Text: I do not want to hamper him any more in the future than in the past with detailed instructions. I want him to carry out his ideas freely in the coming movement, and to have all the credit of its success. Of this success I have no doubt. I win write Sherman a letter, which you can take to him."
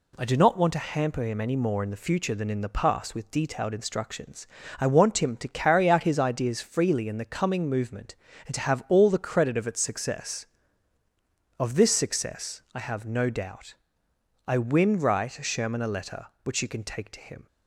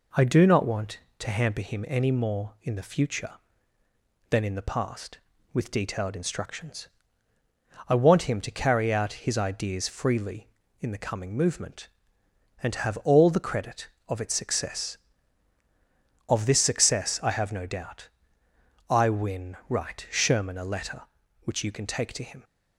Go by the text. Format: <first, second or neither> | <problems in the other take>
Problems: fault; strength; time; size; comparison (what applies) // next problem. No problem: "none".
neither | none